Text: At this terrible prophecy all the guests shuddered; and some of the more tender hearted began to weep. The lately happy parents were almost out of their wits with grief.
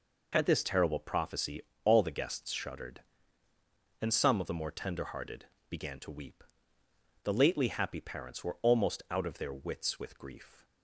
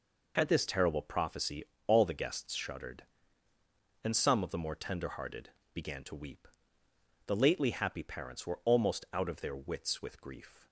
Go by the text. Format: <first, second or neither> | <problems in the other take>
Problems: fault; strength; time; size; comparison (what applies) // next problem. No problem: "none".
neither | pauses between "prophecy" and "all"; slight; the same in both // pauses between "hearted" and "began"; slight; the same in both